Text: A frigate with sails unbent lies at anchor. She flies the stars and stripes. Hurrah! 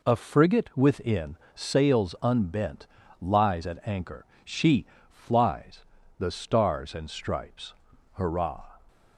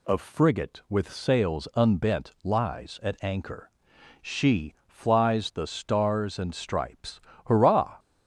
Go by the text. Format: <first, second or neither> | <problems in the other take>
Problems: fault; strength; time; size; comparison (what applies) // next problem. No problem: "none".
second | says "within" for "with"; at 0.7 s // pauses between "unbent" and "lies"; slight; at 2.8 s; 0.32 s long // pauses between "She" and "flies"; slight; at 4.8 s; 0.24 s long // pauses between "flies" and "the"; slight; at 5.8 s; 0.34 s long